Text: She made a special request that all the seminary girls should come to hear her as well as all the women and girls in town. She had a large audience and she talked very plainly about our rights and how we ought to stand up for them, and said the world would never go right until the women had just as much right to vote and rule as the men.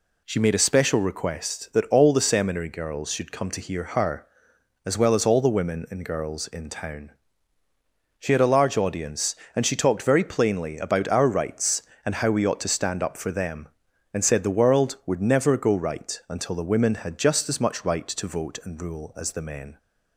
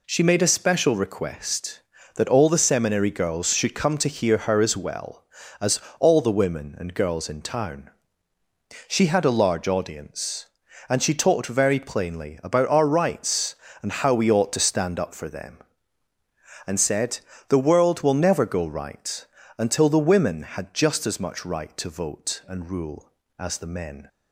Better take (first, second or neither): first